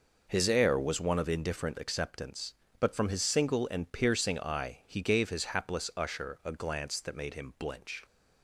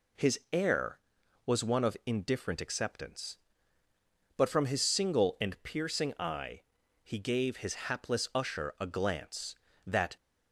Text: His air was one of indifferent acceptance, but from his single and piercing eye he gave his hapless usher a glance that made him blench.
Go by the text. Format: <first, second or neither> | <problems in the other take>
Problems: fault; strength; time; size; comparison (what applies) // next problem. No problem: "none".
first | pauses between "eye" and "he"; at 6.6 s; 0.42 s long // stops before "made him blench"; at 10.1 s